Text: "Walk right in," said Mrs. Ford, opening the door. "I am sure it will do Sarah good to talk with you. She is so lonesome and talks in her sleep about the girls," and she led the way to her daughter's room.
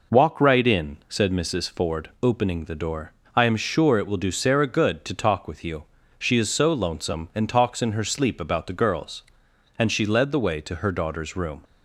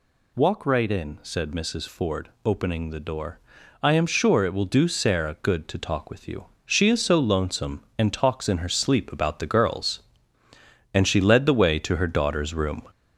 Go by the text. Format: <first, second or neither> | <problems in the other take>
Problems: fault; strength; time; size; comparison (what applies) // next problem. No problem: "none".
first | gets louder; noticeable; throughout; 4.5 dB